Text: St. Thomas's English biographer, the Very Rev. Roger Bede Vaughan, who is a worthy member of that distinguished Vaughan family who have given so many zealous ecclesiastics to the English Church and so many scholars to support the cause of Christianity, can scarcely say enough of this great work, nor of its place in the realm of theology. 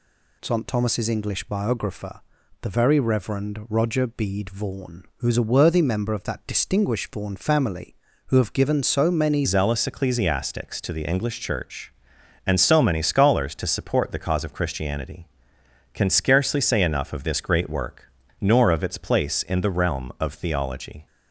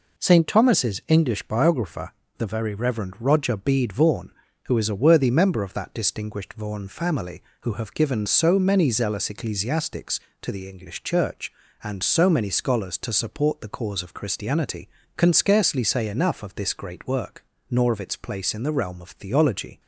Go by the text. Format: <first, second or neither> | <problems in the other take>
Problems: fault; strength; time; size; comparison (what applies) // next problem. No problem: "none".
second | changes voice at "zealous"; from 9.4 s on; 11.6 s long